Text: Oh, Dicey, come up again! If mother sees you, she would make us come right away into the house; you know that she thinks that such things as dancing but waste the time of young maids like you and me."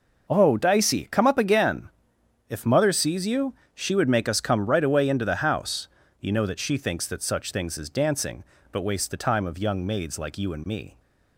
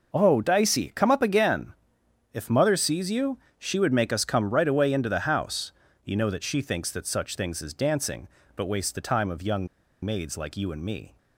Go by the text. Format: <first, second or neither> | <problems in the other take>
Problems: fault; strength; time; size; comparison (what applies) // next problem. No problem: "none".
first | pauses between "young" and "maids"; at 9.6 s; 0.37 s long